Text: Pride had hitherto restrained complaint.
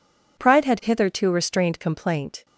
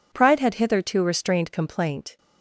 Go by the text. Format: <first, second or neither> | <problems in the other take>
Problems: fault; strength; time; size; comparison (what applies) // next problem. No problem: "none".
neither | none